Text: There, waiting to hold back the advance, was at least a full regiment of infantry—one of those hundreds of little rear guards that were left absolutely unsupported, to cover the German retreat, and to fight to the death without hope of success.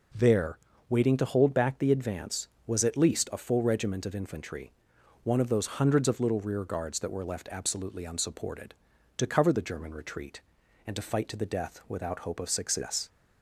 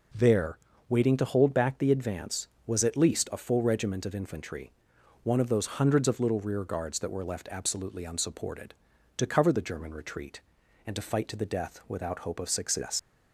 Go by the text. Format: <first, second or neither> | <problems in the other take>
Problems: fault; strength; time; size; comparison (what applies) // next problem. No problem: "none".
first | leaves "success" unfinished; at 12.9 s; 90 ms